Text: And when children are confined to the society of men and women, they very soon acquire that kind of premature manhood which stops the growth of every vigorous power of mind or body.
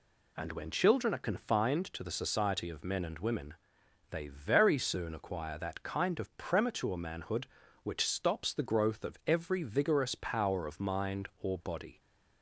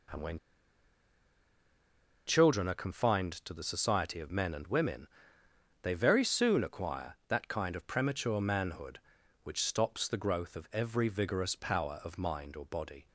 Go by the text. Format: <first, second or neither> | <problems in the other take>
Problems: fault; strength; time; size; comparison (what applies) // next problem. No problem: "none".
first | pauses between "when" and "children"; strong; at 0.3 s; 1.9 s long